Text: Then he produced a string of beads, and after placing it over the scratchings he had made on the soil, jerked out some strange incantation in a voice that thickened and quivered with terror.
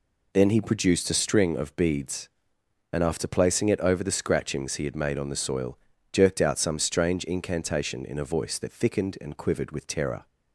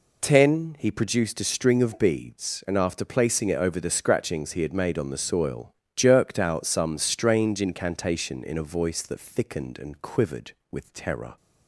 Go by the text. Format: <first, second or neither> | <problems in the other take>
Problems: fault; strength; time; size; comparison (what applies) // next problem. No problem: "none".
first | says "Ten" for "Then"; at 0.2 s